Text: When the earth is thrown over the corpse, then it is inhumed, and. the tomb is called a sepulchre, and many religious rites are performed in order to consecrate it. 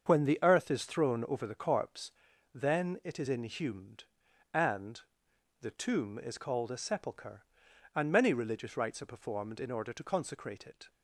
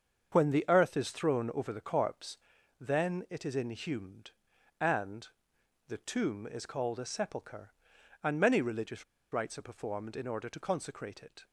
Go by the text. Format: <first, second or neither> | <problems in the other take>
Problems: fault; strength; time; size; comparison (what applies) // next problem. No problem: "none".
first | starts louder than the rest; until 1.3 s; 7 dB; also in the first // pauses between "religious" and "rites"; slight; at 9.0 s; 0.29 s long